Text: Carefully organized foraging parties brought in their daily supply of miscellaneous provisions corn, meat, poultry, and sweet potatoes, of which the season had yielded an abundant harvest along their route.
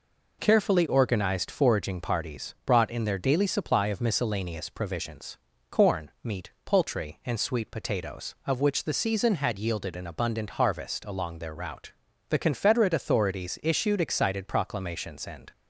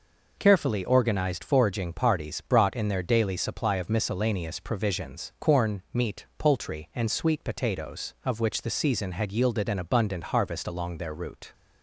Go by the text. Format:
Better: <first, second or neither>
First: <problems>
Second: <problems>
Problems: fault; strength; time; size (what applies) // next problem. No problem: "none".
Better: second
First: pauses between "provisions" and "corn"; slight; at 5.3 s; 0.32 s long // goes on to say "The Confederate authorities issued excited proclamations and"; strong; from 12.2 s on; 3.2 s long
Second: none